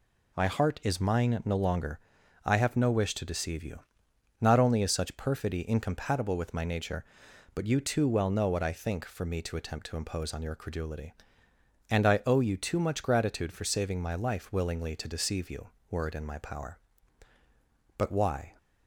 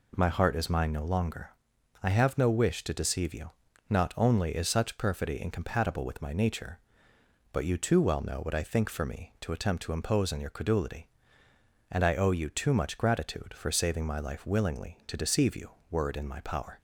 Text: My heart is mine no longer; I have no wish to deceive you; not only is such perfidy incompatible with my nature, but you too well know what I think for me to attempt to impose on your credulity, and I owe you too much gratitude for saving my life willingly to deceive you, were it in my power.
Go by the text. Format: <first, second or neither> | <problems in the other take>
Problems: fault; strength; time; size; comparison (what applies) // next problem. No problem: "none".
second | goes on to say "But why"; from 17.9 s on; 0.56 s long